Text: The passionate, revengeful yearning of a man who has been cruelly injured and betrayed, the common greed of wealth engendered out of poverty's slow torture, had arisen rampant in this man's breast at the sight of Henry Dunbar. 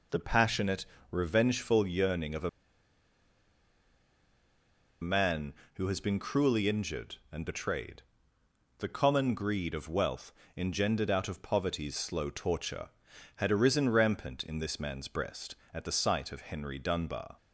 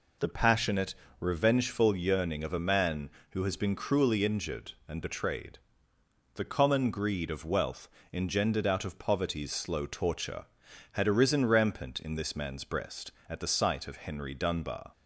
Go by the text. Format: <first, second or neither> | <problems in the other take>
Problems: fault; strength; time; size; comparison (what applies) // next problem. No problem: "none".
second | pauses between "a" and "man"; strong; at 2.4 s; 2.5 s long // pauses between "wealth" and "engendered"; slight; at 10.3 s; 0.24 s long; slight in the second